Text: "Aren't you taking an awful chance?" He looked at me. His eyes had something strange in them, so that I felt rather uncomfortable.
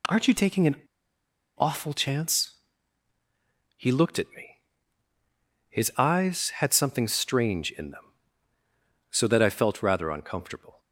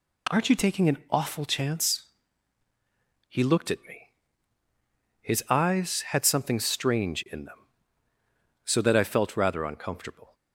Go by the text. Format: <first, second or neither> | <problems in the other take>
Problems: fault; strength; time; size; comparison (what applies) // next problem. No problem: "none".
second | pauses between "an" and "awful"; noticeable; at 0.7 s; 0.81 s long